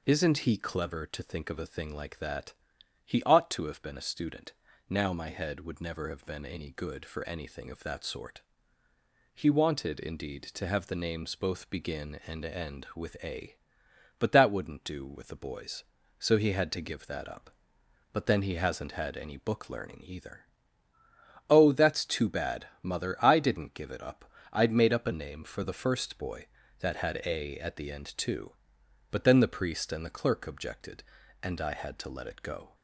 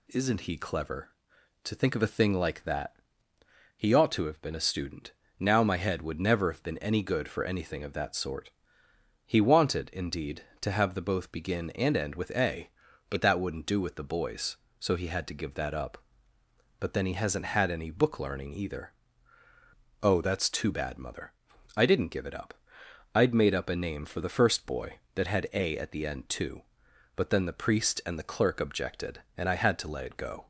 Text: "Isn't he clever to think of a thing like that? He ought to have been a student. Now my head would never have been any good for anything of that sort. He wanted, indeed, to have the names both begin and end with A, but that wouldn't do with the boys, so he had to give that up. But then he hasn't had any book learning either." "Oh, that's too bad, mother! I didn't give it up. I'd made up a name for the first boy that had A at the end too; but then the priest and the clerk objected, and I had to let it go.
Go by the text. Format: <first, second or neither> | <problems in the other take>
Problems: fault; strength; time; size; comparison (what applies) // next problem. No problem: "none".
first | skips "names"; at 11.0 s